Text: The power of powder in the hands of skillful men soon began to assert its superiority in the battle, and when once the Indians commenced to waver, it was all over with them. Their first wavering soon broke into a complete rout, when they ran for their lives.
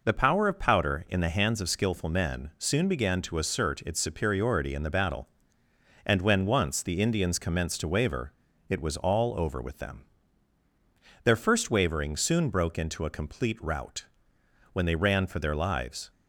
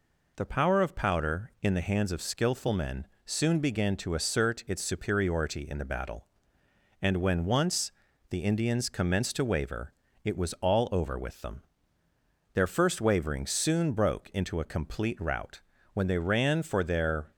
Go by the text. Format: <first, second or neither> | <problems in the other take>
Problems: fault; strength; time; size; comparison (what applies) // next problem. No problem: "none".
first | pauses between "men" and "soon"; slight; at 3.0 s; 0.18 s long // pauses between "once" and "the"; at 7.9 s; 0.38 s long // stops before "lives"; at 17.3 s